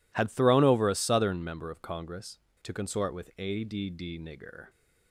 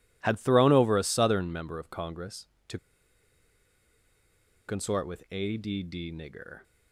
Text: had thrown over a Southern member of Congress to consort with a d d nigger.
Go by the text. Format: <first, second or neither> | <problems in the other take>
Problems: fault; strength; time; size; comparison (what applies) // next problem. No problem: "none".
first | pauses between "to" and "consort"; strong; at 2.7 s; 1.8 s long